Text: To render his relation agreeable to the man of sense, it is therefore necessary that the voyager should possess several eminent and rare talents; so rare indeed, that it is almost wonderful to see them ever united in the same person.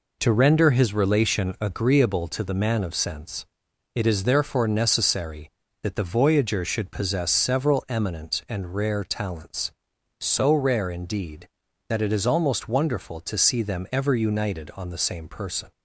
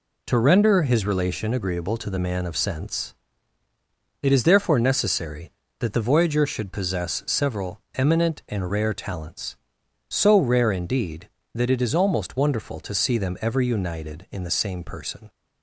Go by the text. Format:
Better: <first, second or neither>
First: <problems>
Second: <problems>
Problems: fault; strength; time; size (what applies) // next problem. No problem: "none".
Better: second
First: says "on" for "in"; at 14.7 s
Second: none